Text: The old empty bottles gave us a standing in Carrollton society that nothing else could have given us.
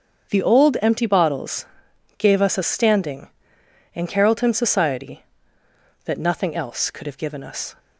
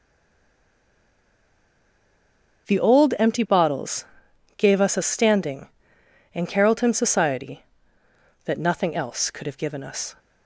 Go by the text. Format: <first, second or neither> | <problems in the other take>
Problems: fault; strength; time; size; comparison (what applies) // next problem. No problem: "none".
first | stays silent before the first word; strong; until 2.6 s; 2.6 s long // starts louder than the rest; strong; until 3.7 s; 7 dB; strong in the first // pauses between "bottles" and "gave"; noticeable; at 4.0 s; 0.52 s long; noticeable in the first